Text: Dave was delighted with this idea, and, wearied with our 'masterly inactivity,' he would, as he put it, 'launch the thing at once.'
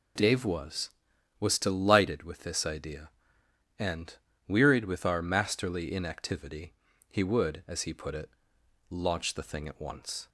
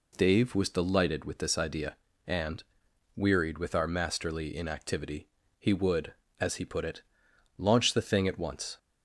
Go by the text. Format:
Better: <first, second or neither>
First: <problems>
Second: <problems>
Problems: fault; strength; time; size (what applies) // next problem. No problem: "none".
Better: second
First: says "was" twice; at 1.3 s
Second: none